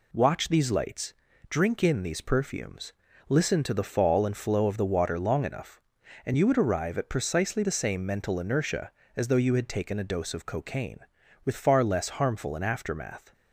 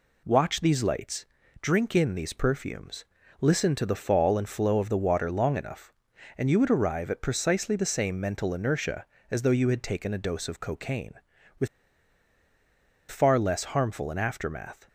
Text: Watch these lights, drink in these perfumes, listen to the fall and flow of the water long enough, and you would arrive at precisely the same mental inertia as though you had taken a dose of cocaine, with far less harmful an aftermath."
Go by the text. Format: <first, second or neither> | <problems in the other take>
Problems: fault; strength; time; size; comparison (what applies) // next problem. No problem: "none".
first | pauses between "with" and "far"; strong; at 11.6 s; 1.4 s long